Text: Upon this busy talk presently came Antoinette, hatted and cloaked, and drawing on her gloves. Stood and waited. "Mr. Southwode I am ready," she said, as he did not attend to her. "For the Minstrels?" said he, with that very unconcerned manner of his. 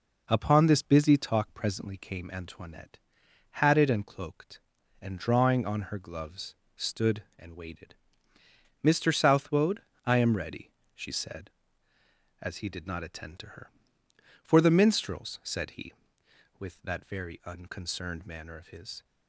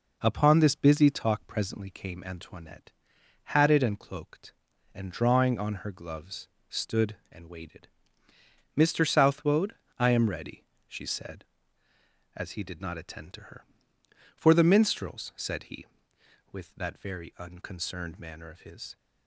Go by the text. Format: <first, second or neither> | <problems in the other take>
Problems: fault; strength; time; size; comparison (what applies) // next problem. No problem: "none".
neither | pauses between "Southwode" and "I"; slight; the same in both